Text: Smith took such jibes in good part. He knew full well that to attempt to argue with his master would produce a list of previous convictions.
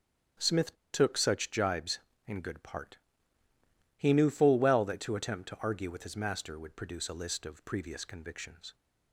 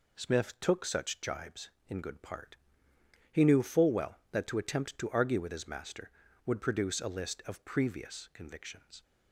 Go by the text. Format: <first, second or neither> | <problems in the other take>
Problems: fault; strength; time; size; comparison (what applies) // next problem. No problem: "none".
second | starts louder than the rest; strong; until 1.5 s; 9 dB // pauses between "Smith" and "took"; slight; at 0.7 s; 0.17 s long